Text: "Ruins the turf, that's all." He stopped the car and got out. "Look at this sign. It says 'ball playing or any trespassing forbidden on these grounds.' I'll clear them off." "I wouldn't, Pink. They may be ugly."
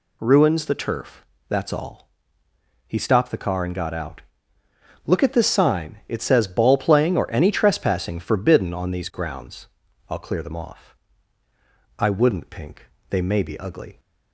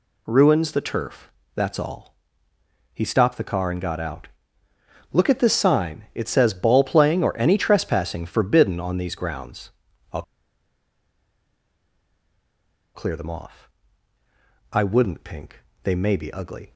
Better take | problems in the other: first | pauses between "I'll" and "clear"; strong; at 10.2 s; 2.7 s long

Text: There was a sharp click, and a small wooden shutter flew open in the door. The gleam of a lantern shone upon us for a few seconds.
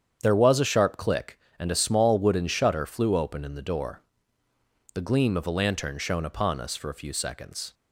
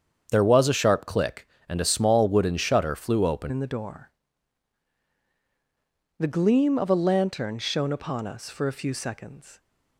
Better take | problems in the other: first | starts louder than the rest; strong; until 1.3 s; 7.5 dB; strong in the first // changes voice at "in"; from 3.4 s on; 6.1 s long

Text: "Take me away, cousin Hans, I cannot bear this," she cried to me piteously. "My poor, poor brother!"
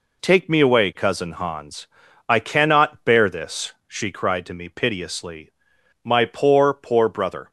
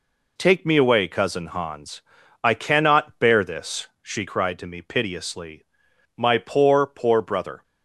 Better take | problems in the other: neither | none

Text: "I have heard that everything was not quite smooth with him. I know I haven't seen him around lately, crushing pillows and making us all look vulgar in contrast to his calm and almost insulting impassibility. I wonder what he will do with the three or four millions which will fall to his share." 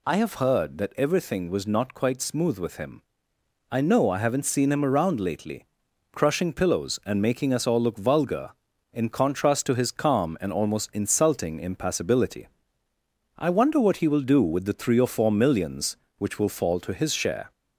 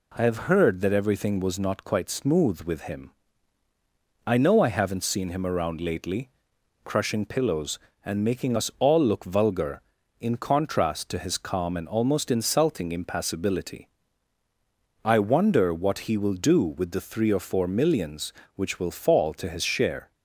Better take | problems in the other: neither | none

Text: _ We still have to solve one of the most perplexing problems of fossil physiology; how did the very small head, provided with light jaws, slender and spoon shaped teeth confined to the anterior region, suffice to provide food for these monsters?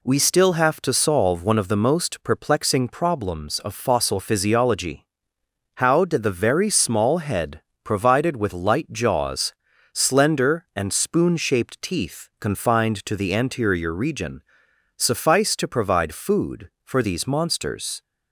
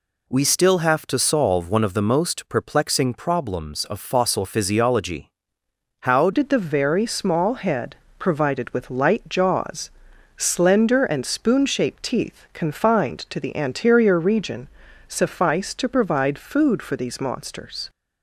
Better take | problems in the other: first | changes voice at "did"; from 6.3 s on; 11.5 s long

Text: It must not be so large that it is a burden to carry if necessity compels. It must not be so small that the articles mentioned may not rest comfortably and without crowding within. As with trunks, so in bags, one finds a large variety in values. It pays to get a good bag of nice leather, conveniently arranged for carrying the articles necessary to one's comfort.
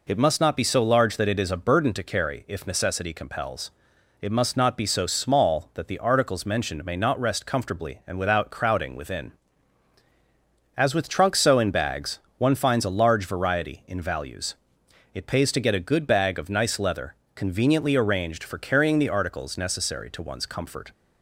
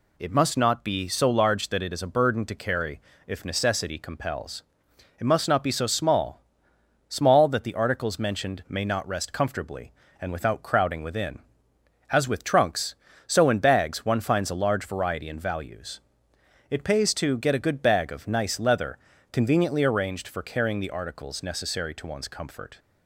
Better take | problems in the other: first | pauses between "carry" and "if"; slight; at 3.0 s; 0.26 s long // says "small" twice; at 7.0 s

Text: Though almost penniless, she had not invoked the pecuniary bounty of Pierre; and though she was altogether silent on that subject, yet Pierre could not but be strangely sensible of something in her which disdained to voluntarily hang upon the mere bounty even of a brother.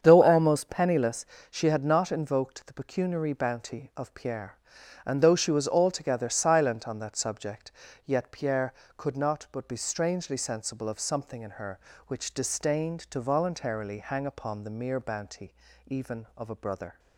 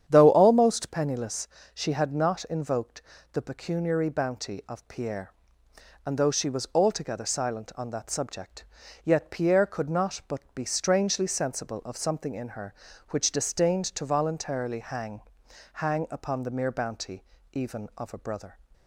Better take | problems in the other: first | starts louder than the rest; strong; until 1.0 s; 9 dB; strong in the first // pauses between "invoked" and "the"; slight; at 3.0 s; 0.32 s long // says "hang" twice; at 15.7 s // pauses between "bounty" and "even"; slight; at 17.2 s; 0.26 s long; slight in the first

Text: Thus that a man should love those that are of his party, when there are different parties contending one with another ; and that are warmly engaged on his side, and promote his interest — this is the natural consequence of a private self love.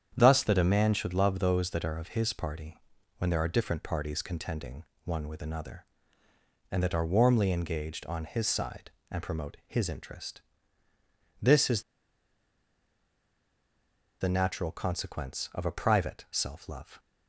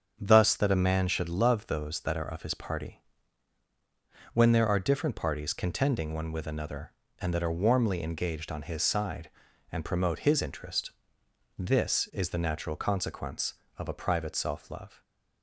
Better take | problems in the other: second | starts louder than the rest; strong; until 1.1 s; 8.5 dB; strong in the second // pauses between "contending" and "one"; slight; at 4.8 s; 0.22 s long // pauses between "is" and "the"; strong; at 11.8 s; 2.3 s long

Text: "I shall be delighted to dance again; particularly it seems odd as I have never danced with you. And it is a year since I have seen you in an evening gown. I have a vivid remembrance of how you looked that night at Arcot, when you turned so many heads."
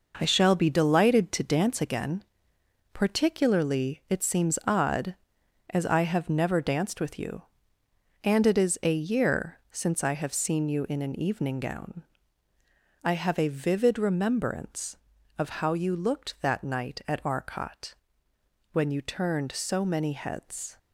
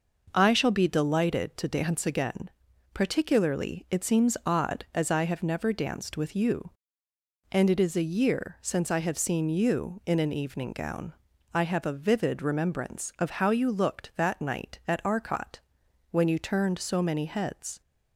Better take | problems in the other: second | gets quieter; strong; throughout; 7 dB

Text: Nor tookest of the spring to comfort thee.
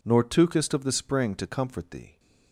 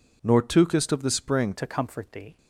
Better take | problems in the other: first | changes voice at "to"; from 1.5 s on; 0.8 s long

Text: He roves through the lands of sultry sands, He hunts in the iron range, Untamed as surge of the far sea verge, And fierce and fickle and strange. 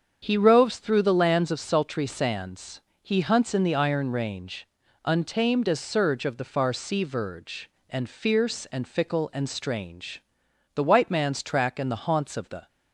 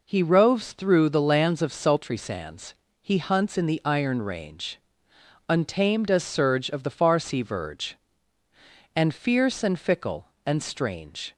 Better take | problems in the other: second | starts louder than the rest; strong; until 1.2 s; 7.5 dB // goes on to say "The white man's track and the haunts of the"; strong; from 10.7 s on; 1.9 s long

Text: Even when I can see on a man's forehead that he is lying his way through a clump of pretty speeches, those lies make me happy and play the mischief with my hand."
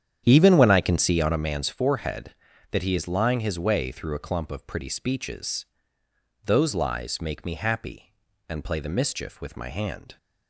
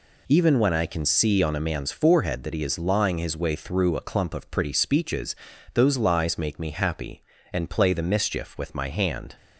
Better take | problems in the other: second | starts louder than the rest; strong; until 1.5 s; 9 dB

